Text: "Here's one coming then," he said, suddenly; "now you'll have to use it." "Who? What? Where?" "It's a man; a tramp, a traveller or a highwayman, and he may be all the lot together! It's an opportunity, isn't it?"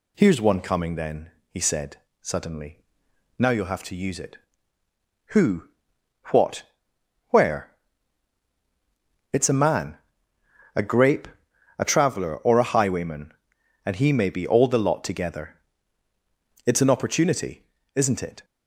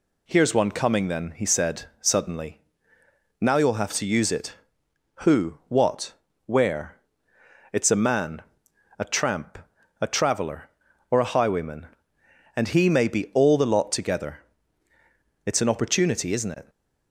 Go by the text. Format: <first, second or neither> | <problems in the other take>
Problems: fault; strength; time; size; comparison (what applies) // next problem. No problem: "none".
second | says "grape" for "tramp"; at 10.8 s